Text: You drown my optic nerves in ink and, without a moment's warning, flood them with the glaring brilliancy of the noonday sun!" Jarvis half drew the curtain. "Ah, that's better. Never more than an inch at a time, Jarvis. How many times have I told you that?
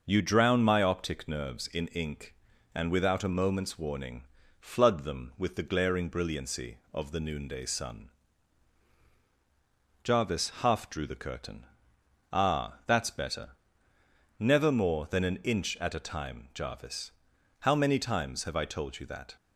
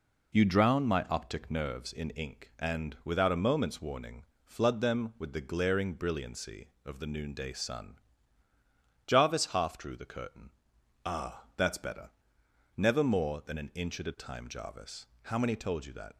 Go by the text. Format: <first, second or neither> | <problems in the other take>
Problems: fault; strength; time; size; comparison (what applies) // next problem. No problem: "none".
first | skips "times have I"; at 15.5 s